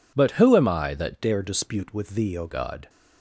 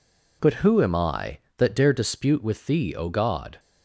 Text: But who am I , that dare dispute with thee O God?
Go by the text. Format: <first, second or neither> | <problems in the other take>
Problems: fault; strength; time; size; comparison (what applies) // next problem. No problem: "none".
second | changes voice from "dare" to "O"; from 1.1 to 2.4 s; 1.3 s long